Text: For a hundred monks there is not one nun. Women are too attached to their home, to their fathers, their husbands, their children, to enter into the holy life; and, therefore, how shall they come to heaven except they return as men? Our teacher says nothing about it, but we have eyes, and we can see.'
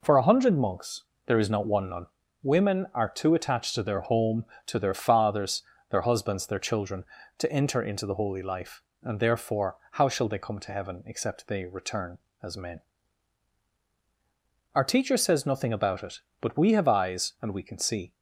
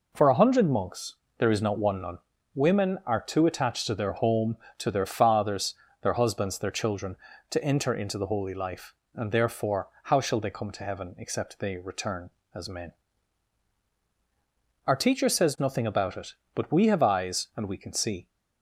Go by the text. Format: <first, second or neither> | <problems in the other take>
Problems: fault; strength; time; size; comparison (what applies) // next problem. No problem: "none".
neither | pauses between "monks" and "there"; slight; the same in both